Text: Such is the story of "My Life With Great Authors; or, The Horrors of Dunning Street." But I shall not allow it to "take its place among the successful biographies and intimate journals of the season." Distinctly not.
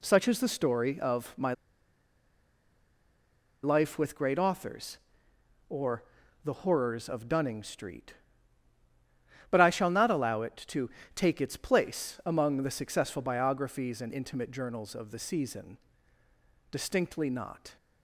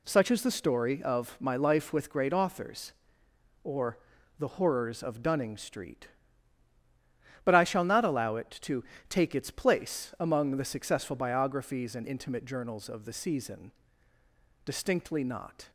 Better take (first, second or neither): second